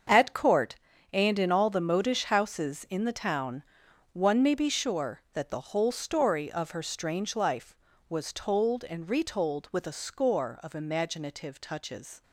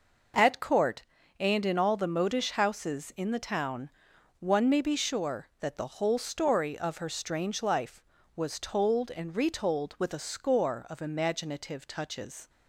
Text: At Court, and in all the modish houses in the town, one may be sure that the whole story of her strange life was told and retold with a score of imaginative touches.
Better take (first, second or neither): second